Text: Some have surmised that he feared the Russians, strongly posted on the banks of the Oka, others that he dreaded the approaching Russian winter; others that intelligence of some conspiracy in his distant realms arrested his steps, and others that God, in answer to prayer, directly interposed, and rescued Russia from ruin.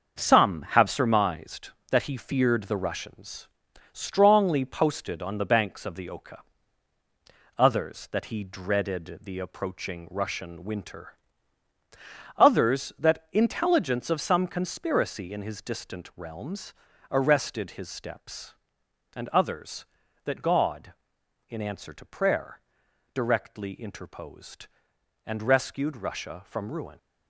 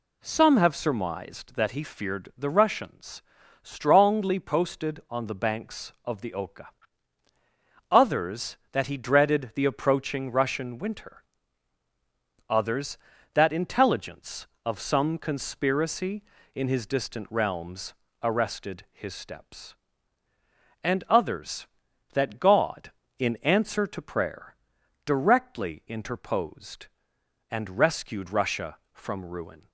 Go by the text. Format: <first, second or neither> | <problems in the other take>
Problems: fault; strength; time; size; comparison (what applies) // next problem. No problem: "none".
second | gets quieter; throughout; 6.5 dB // pauses between "realms" and "arrested"; at 16.7 s; 0.38 s long; slight in the second